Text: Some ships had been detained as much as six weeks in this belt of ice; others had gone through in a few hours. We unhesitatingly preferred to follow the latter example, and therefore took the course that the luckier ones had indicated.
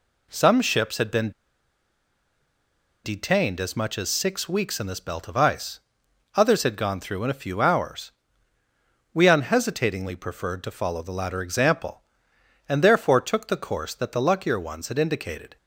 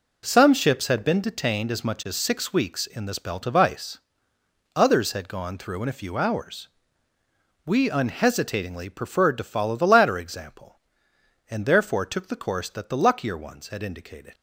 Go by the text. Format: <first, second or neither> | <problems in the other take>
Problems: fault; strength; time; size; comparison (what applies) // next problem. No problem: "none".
second | pauses between "been" and "detained"; strong; at 1.3 s; 1.7 s long